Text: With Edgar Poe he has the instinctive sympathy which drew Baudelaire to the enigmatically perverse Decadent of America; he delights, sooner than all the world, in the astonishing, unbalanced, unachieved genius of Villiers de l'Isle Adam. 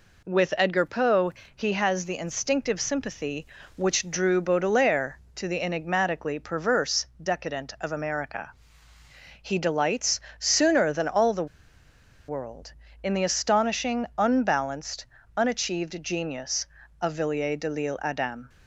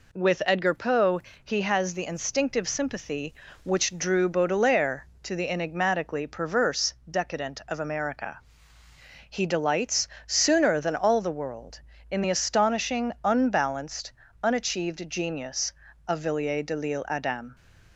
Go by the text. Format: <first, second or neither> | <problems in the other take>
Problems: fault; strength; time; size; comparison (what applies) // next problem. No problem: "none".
second | pauses between "Poe" and "he"; slight; at 1.3 s; 0.24 s long; slight in the second // pauses between "perverse" and "Decadent"; slight; at 7.0 s; 0.16 s long; slight in the second // pauses between "the" and "world"; noticeable; at 11.4 s; 0.82 s long